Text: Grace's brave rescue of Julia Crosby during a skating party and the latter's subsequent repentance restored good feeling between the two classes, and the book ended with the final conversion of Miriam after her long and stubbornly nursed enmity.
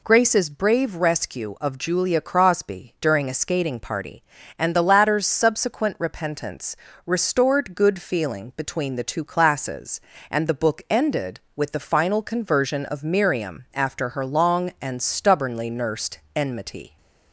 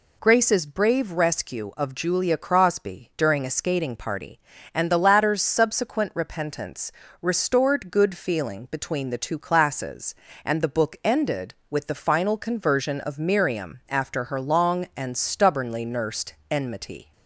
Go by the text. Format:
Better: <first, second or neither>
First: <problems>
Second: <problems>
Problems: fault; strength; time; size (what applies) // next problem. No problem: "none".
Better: neither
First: pauses between "repentance" and "restored"; slight; at 6.7 s; 0.30 s long // pauses between "nursed" and "enmity"; slight; at 16.1 s; 0.16 s long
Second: pauses between "repentance" and "restored"; slight; at 6.9 s; 0.30 s long // pauses between "nursed" and "enmity"; slight; at 16.3 s; 0.16 s long